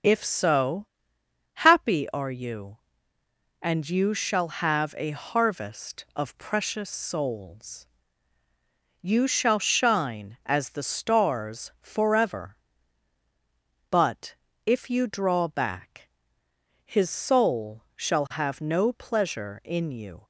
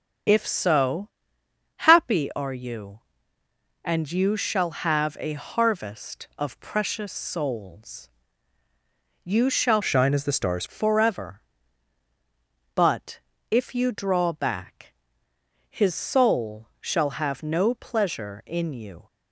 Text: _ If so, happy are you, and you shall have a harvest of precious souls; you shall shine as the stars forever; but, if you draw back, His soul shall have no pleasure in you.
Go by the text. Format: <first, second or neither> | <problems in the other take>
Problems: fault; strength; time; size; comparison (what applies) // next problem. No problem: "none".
first | starts louder than the rest; strong; until 1.9 s; 7.5 dB; strong in the first // changes voice from "shine" to "stars"; from 9.8 to 10.6 s; 0.8 s long